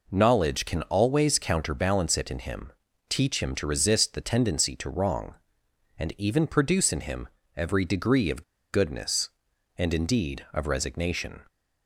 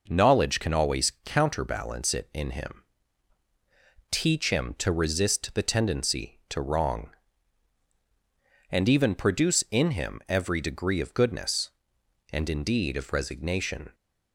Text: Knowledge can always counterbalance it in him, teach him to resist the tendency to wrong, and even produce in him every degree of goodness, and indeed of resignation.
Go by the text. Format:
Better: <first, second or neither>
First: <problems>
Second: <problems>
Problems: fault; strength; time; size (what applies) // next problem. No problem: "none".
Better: second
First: pauses between "him" and "every"; slight; at 7.2 s; 0.30 s long // pauses between "of" and "goodness"; slight; at 8.4 s; 0.29 s long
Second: none